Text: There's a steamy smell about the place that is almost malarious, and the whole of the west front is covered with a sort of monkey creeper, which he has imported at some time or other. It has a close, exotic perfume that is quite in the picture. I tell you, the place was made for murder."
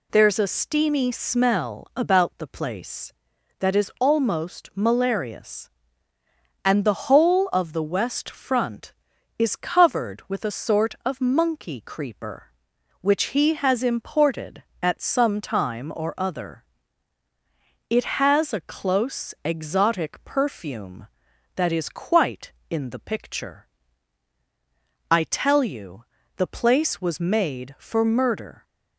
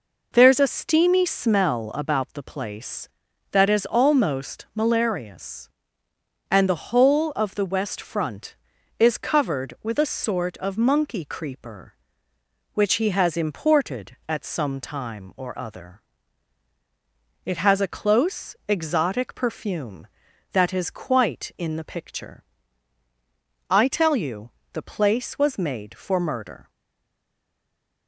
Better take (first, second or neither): first